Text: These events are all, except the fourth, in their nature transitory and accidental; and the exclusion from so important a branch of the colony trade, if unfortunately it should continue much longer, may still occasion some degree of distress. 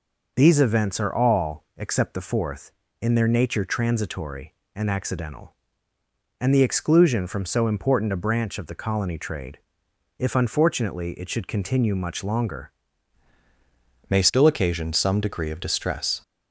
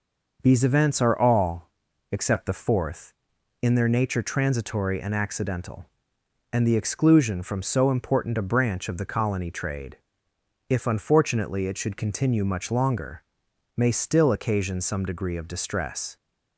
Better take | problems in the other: second | changes voice at "may"; from 14.0 s on; 2.2 s long

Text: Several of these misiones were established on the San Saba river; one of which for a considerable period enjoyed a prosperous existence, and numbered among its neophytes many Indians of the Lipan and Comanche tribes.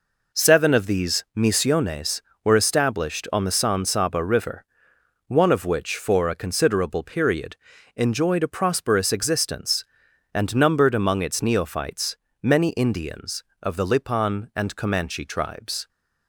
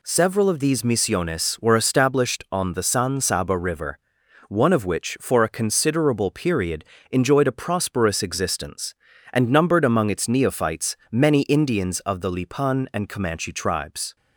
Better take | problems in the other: second | says "Seven" for "Several"; at 0.3 s // pauses between "period" and "enjoyed"; at 7.5 s; 0.40 s long; slight in the second // pauses between "neophytes" and "many"; slight; at 12.1 s; 0.26 s long; slight in the second

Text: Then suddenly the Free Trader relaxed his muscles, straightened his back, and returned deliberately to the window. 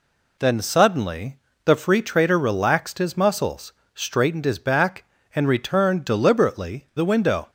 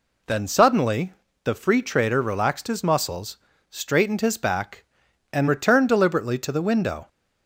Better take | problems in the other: second | pauses between "suddenly" and "the"; slight; at 1.3 s; 0.28 s long; slight in the second // skips "to"; at 6.9 s

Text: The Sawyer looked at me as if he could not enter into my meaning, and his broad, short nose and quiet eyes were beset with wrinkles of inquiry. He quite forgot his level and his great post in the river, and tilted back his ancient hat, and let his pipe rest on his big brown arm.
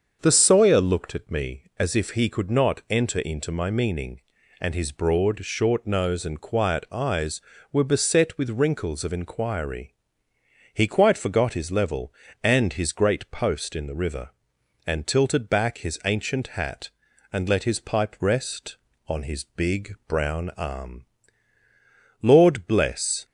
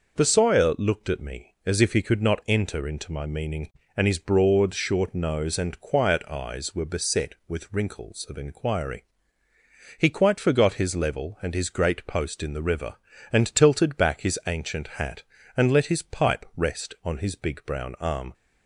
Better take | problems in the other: second | starts louder than the rest; until 1.2 s; 7 dB // goes on to say "Lord bless"; noticeable; from 22.2 s on; 1.0 s long

